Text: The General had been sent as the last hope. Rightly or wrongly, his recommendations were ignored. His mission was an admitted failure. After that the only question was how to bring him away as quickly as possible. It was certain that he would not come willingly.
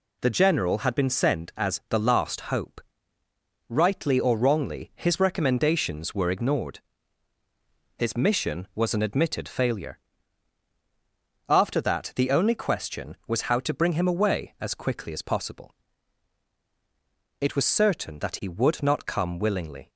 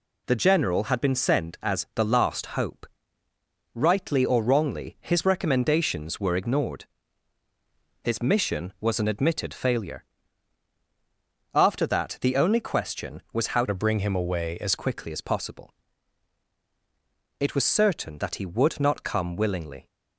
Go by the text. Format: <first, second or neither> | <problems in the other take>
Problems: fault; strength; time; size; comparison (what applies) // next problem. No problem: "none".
first | changes voice from "to" to "as"; from 13.6 to 14.7 s; 1.1 s long